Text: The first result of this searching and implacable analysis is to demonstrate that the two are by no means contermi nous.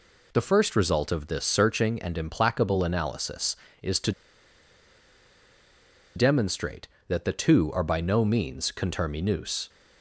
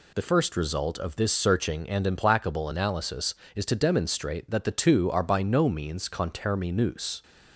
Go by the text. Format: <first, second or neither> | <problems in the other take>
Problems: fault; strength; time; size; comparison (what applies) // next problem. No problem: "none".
second | pauses between "to" and "demonstrate"; strong; at 4.1 s; 2.0 s long